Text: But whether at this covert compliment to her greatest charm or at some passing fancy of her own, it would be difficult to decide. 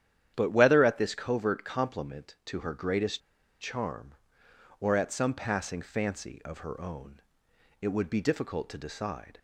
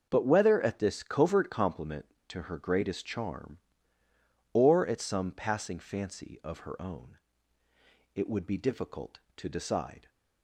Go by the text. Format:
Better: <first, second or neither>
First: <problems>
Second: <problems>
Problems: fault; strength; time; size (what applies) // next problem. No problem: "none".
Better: second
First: starts louder than the rest; strong; until 1.3 s; 10 dB // pauses between "greatest" and "charm"; at 3.2 s; 0.40 s long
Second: starts louder than the rest; until 1.1 s; 6.5 dB